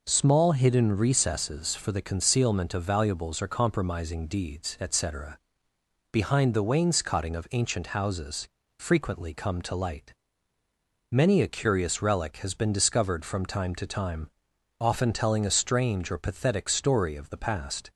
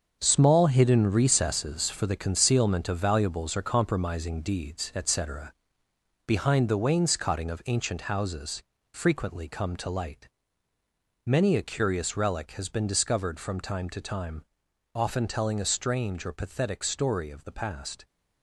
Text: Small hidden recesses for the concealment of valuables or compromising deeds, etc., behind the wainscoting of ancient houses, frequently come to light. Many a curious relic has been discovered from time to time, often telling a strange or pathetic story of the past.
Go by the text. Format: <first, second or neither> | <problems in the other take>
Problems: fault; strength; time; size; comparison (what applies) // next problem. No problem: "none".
first | gets quieter; strong; throughout; 9 dB